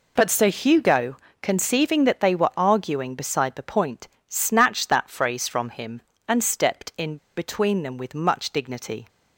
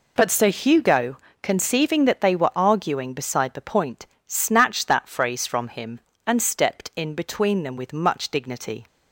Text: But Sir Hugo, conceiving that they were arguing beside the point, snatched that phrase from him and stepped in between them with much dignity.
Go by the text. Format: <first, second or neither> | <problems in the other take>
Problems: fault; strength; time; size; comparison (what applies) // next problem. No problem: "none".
second | pauses between "in" and "between"; slight; at 7.1 s; 0.20 s long